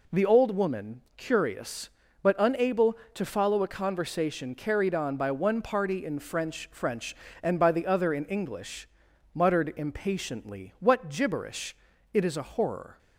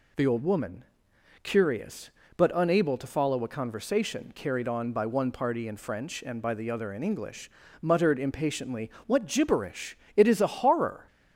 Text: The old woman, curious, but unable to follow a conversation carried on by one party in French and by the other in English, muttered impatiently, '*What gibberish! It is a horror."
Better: second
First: says "French" twice; at 6.7 s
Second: none

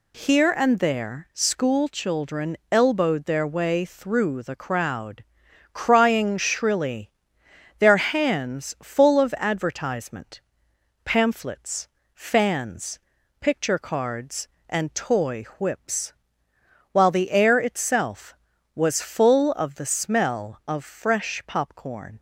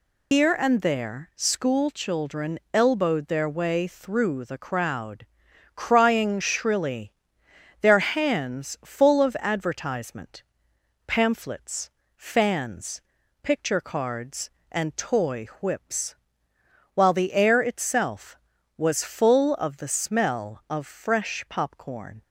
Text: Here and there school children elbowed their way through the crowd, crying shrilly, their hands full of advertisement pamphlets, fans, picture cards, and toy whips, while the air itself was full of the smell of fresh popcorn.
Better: first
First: pauses between "children" and "elbowed"; slight; at 2.5 s; 0.16 s long // pauses between "advertisement" and "pamphlets"; noticeable; at 10.3 s; 0.64 s long // pauses between "toy" and "whips"; slight; at 15.4 s; 0.16 s long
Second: loses the start of "Here"; at 0.3 s; 145 ms // pauses between "children" and "elbowed"; slight; at 2.5 s; 0.16 s long // pauses between "advertisement" and "pamphlets"; noticeable; at 10.4 s; 0.64 s long // pauses between "toy" and "whips"; slight; at 15.4 s; 0.16 s long

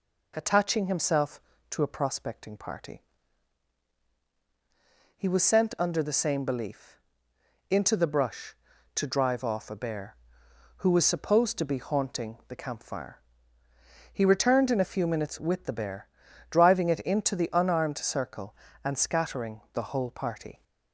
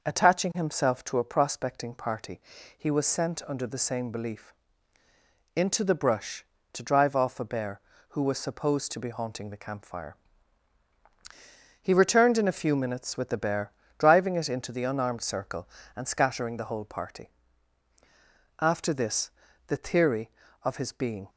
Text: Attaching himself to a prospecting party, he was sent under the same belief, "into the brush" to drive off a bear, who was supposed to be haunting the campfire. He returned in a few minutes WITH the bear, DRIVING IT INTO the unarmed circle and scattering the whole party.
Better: first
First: none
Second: goes on to say "After this the theory of his being"; strong; from 18.5 s on; 2.7 s long

